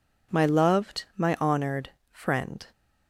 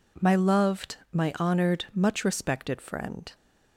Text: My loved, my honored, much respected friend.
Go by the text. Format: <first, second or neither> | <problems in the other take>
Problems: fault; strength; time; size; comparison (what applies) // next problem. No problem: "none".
second | skips "much respected"; at 2.0 s